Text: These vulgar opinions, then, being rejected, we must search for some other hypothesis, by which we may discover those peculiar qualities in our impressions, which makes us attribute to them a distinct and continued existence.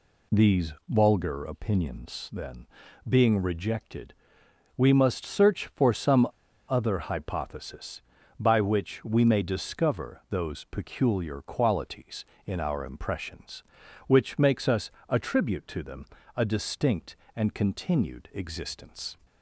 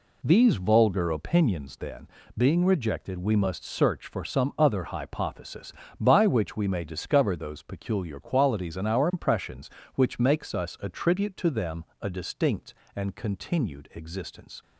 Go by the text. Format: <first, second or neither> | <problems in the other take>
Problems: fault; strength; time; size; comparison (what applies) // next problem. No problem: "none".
second | pauses between "some" and "other"; at 6.2 s; 0.44 s long // pauses between "us" and "attribute"; slight; at 14.8 s; 0.18 s long // pauses between "them" and "a"; slight; at 16.0 s; 0.28 s long; slight in the second